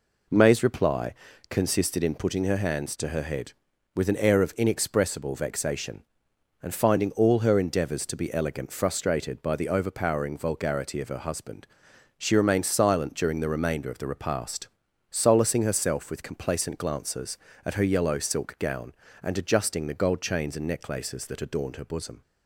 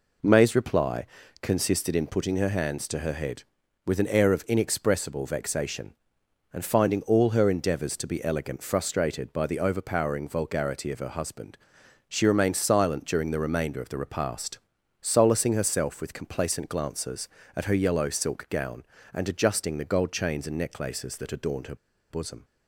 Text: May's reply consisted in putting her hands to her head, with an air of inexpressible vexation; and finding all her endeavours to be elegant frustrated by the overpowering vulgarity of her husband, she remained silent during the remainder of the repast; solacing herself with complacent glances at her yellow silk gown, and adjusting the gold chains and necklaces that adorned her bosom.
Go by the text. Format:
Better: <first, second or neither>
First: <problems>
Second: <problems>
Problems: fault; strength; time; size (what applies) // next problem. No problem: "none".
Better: first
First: pauses between "reply" and "consisted"; slight; at 1.1 s; 0.36 s long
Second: pauses between "reply" and "consisted"; slight; at 1.0 s; 0.36 s long // pauses between "her" and "bosom"; slight; at 21.7 s; 0.34 s long